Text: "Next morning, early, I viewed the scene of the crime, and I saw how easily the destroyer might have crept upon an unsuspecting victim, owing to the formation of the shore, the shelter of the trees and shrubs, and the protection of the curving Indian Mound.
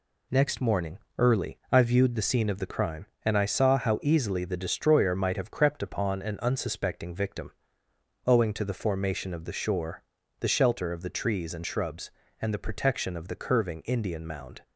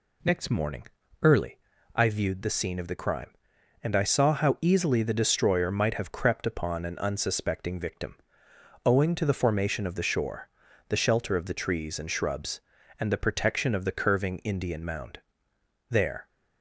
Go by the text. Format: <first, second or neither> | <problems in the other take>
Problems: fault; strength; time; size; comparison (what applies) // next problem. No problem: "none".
first | goes on to say "There"; slight; from 15.8 s on; 0.38 s long